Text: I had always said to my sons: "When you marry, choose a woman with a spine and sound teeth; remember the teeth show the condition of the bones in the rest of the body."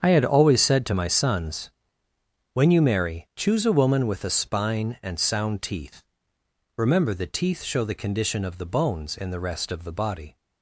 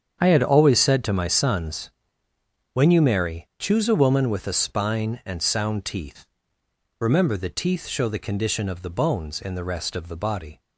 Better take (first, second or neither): neither